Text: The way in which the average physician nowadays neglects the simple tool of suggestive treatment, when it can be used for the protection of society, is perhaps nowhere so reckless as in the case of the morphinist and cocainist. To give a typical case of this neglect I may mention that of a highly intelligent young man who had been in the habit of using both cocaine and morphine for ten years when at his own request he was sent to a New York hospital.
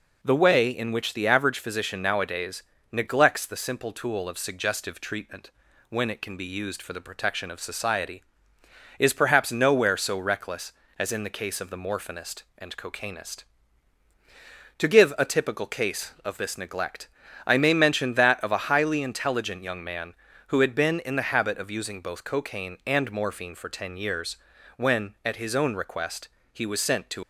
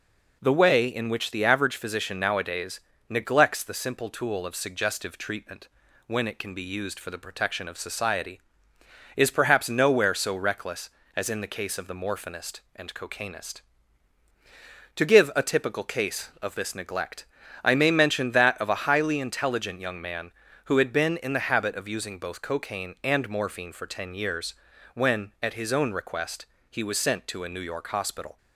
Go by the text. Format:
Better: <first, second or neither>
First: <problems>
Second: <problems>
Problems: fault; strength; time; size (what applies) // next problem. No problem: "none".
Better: second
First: pauses between "nowadays" and "neglects"; slight; at 2.6 s; 0.30 s long // pauses between "neglect" and "I"; at 17.0 s; 0.40 s long // pauses between "years" and "when"; at 24.3 s; 0.40 s long // pauses between "request" and "he"; slight; at 26.2 s; 0.24 s long // stops before "a New York hospital"; at 27.2 s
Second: pauses between "nowadays" and "neglects"; slight; at 2.7 s; 0.30 s long // pauses between "neglect" and "I"; at 17.2 s; 0.40 s long // pauses between "years" and "when"; at 24.5 s; 0.40 s long // pauses between "request" and "he"; slight; at 26.4 s; 0.24 s long